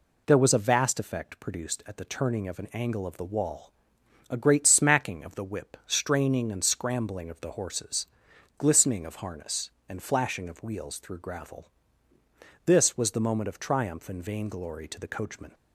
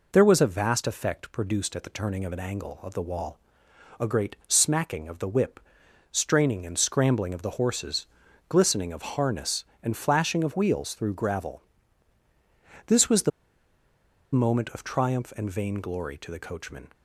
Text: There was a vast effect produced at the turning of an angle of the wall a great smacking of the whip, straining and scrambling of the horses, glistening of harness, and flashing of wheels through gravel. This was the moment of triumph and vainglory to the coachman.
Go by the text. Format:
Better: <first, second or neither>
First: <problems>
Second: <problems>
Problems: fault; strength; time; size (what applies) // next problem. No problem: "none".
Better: first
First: pauses between "wall" and "a"; noticeable; at 3.7 s; 0.56 s long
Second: pauses between "wall" and "a"; noticeable; at 3.3 s; 0.62 s long // pauses between "the" and "moment"; at 13.3 s; 1.0 s long